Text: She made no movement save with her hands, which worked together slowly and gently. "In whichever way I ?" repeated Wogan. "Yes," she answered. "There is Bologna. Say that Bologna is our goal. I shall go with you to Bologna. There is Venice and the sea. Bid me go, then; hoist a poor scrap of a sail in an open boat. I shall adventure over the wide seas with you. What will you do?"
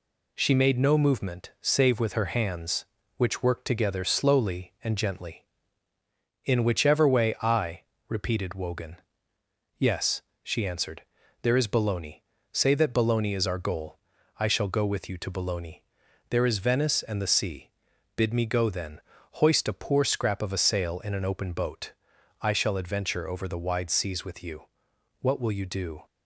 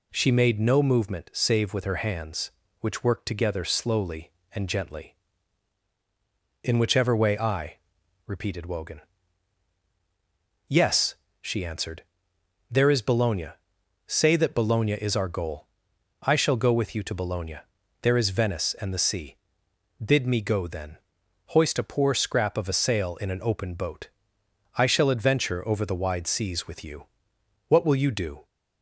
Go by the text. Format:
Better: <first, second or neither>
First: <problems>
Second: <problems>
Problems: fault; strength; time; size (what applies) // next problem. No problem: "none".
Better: neither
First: none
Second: none